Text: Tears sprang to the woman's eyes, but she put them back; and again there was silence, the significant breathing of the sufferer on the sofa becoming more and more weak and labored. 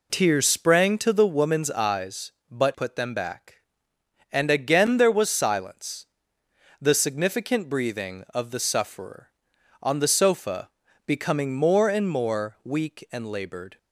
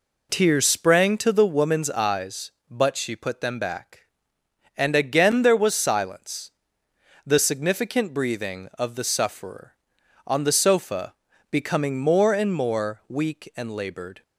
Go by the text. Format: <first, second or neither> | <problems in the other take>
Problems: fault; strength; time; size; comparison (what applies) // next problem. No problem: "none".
second | skips "she"; at 2.7 s // pauses between "sofa" and "becoming"; slight; at 10.6 s; 0.36 s long; slight in the second